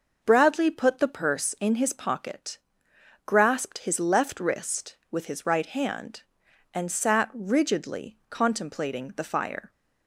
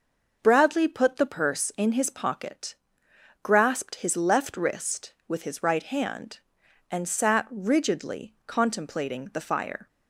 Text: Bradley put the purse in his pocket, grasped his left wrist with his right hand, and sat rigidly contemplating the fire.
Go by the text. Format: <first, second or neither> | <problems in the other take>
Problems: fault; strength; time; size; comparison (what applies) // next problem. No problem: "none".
neither | none